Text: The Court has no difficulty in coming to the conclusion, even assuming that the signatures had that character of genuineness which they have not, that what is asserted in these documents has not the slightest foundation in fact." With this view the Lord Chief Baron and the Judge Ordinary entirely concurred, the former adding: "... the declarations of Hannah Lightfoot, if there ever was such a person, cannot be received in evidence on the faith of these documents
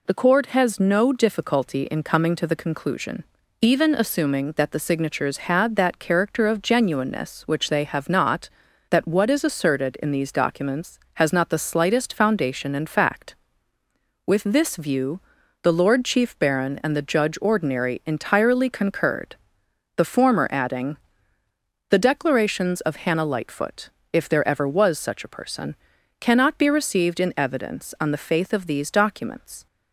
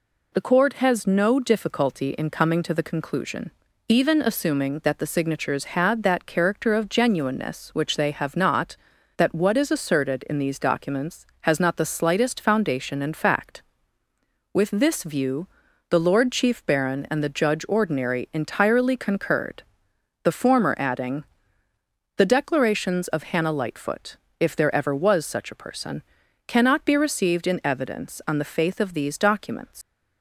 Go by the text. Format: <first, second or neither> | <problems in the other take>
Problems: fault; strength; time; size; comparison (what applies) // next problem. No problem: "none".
first | pauses between "view" and "the"; at 15.4 s; 0.42 s long; also in the first // leaves "documents" unfinished; at 29.8 s; 120 ms